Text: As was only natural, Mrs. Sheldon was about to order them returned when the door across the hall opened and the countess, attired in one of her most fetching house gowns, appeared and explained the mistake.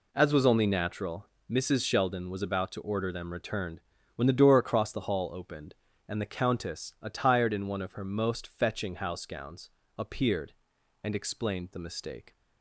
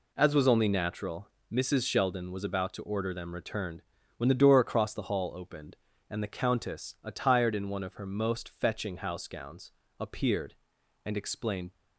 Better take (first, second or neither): first